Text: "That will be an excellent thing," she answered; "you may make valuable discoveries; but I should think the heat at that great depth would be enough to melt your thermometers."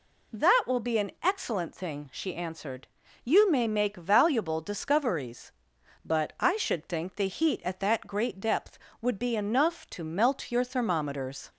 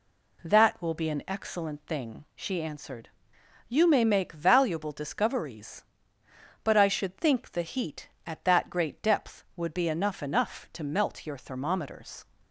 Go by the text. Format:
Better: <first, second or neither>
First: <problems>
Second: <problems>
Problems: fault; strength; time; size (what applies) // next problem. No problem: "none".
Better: first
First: none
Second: says "enough" twice; at 10.2 s